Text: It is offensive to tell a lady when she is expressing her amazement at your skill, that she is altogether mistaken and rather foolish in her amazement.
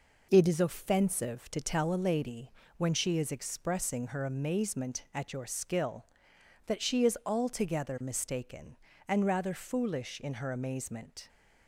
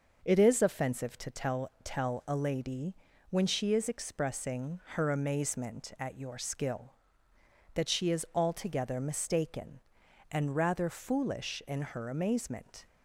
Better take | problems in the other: first | says "tell" twice; at 1.8 s // pauses between "lady" and "when"; slight; at 2.9 s; 0.36 s long; slight in the first // pauses between "expressing" and "her"; slight; at 4.7 s; 0.16 s long

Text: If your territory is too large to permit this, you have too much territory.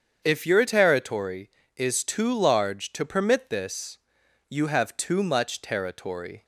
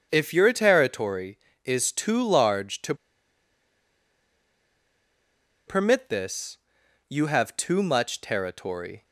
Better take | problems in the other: first | starts louder than the rest; strong; until 1.1 s; 7 dB; strong in the first // pauses between "to" and "permit"; strong; at 2.9 s; 2.7 s long

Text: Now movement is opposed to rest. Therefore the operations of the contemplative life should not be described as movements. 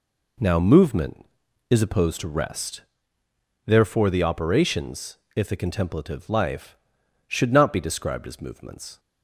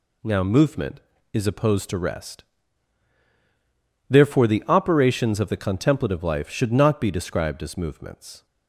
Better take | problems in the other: second | says "if" for "of"; at 5.3 s

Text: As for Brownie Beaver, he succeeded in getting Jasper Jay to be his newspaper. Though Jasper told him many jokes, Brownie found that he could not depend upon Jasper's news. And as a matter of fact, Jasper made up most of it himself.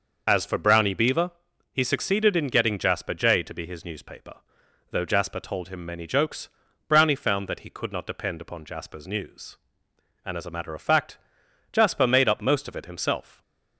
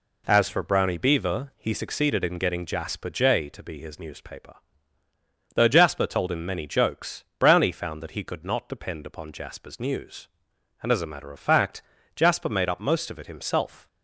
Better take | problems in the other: second | loses the start of "As"; at 0.2 s; 45 ms

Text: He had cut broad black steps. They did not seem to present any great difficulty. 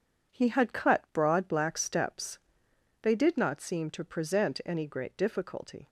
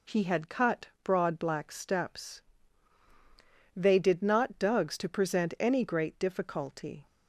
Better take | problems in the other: first | says "dugs" for "seem"; at 4.5 s

